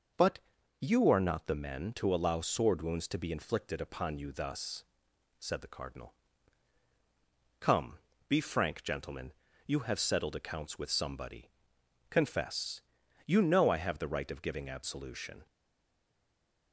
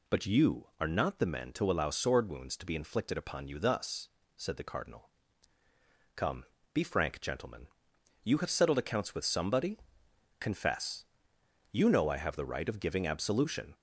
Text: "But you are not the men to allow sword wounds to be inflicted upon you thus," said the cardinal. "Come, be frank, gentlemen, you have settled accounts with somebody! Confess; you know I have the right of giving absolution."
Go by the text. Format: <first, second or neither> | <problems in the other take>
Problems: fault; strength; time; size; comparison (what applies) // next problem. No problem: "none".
second | pauses between "But" and "you"; at 0.3 s; 0.42 s long // stays silent after the last word; noticeable; from 15.4 s on; 1.3 s long